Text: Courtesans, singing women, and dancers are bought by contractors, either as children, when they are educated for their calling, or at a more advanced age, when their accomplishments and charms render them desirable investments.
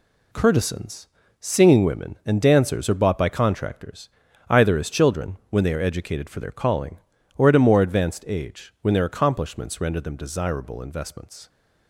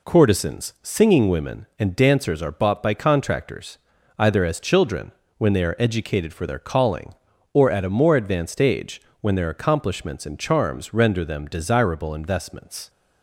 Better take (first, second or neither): second